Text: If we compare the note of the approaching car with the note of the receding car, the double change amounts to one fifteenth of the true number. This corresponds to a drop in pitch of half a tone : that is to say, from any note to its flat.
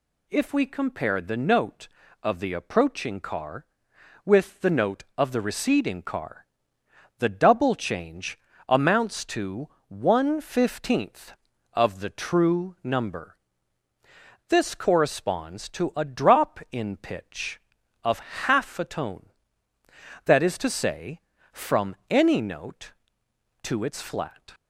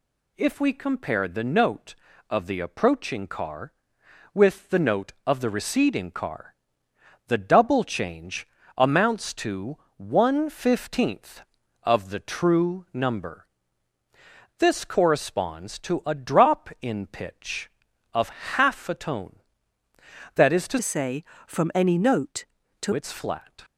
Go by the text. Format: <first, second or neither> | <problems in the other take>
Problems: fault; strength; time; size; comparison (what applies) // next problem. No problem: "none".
first | pauses between "change" and "amounts"; slight; at 8.4 s; 0.30 s long; slight in the first // pauses between "to" and "one"; slight; at 9.7 s; 0.20 s long; slight in the first // pauses between "of" and "half"; slight; at 18.2 s; 0.26 s long; slight in the first // changes voice from "say" to "to"; from 20.8 to 22.9 s; 2.1 s long